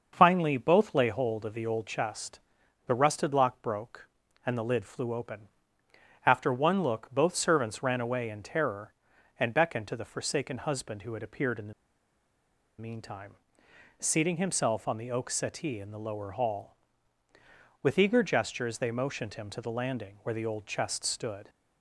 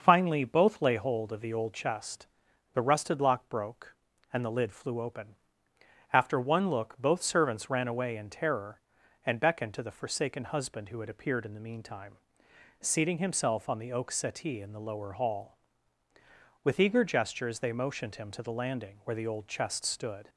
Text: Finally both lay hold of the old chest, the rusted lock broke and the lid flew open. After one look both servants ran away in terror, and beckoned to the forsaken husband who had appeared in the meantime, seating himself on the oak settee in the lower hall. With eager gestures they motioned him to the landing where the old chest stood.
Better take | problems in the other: second | starts louder than the rest; until 1.1 s; 6 dB; also in the second // pauses between "the" and "meantime"; at 11.7 s; 1.0 s long

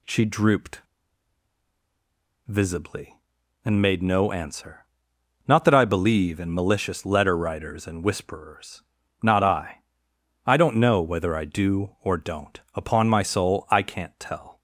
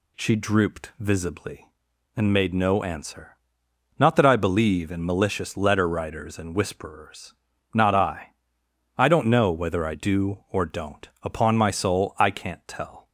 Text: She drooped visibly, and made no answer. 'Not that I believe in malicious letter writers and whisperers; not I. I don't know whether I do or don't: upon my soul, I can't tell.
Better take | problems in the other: second | pauses between "drooped" and "visibly"; strong; at 0.8 s; 1.6 s long

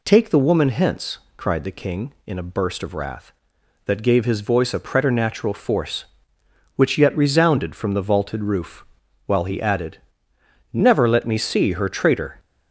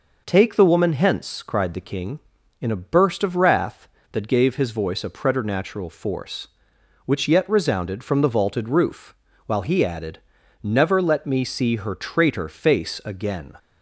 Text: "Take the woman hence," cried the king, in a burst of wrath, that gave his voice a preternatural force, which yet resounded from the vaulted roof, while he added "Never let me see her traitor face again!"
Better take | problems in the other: second | pauses between "added" and "Never"; noticeable; at 9.9 s; 0.76 s long; also in the second // stops before "face again"; at 12.3 s

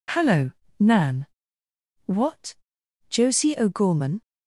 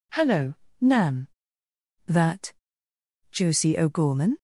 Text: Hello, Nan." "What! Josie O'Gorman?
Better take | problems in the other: first | says "That" for "What"; at 2.0 s

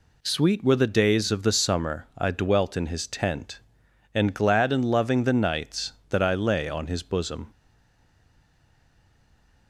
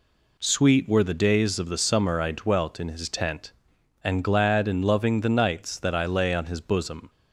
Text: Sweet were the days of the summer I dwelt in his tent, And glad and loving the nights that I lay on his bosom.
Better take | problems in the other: second | stays silent after the last word; from 7.5 s on; 2.1 s long

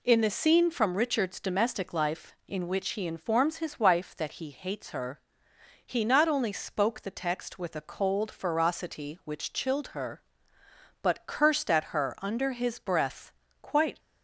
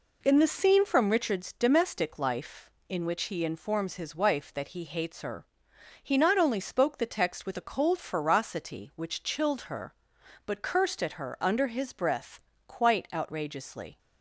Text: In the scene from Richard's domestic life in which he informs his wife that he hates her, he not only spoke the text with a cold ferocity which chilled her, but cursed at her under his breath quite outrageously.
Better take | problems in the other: second | pauses between "breath" and "quite"; slight; at 13.3 s; 0.30 s long; slight in the second // stops before "outrageously"; at 13.9 s

